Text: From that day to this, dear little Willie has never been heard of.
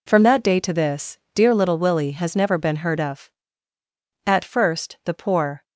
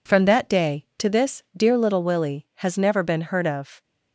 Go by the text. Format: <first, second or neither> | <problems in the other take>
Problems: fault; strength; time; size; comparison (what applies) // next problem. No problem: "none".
second | goes on to say "At first the poor"; from 4.2 s on; 1.3 s long